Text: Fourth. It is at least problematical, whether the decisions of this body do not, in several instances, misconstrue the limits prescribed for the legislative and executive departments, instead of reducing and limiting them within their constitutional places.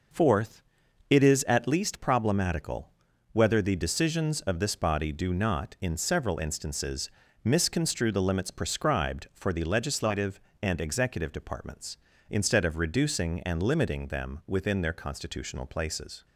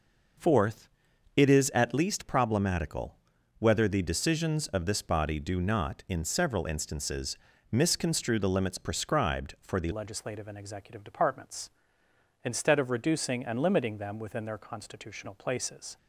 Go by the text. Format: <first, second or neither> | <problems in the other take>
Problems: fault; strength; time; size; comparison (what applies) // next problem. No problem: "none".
first | changes voice at "legislative"; from 9.9 s on; 6.0 s long